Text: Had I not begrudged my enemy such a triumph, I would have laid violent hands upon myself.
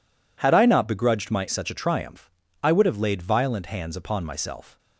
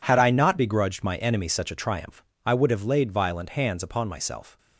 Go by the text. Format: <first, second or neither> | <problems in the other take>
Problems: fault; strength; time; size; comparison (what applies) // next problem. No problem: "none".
second | skips "enemy"; at 1.4 s